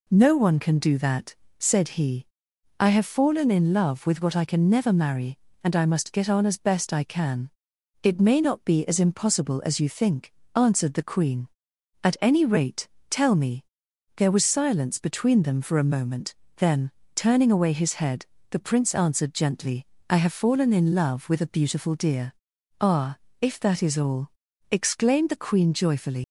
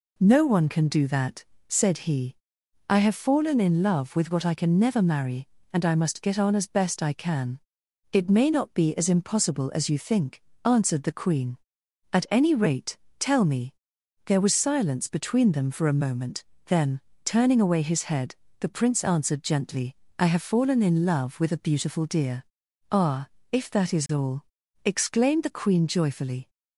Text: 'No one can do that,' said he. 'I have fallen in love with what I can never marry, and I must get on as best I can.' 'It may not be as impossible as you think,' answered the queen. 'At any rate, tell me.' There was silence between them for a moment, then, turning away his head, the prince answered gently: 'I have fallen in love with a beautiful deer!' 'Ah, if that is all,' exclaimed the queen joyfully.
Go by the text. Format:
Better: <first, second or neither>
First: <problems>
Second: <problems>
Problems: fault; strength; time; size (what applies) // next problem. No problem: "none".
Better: second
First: leaves "joyfully" unfinished; at 26.2 s; 115 ms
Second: none